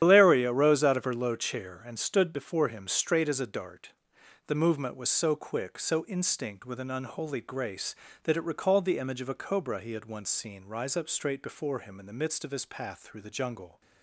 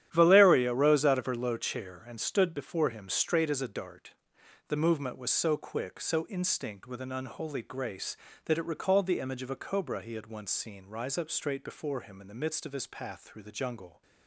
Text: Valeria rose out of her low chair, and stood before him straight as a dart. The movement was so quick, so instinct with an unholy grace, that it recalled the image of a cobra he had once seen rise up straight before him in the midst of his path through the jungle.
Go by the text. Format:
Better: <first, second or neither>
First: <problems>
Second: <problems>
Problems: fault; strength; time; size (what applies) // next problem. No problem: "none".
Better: second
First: loses the start of "Valeria"; at 0.0 s; 115 ms // starts louder than the rest; strong; until 1.0 s; 10 dB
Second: starts louder than the rest; strong; until 1.1 s; 10.5 dB